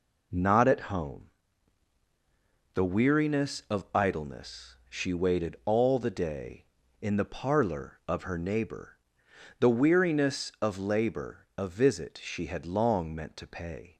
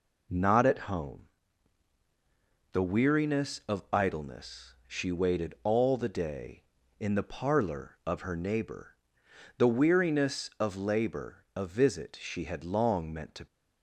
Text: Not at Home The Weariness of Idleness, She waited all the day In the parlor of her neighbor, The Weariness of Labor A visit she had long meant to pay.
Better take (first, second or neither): first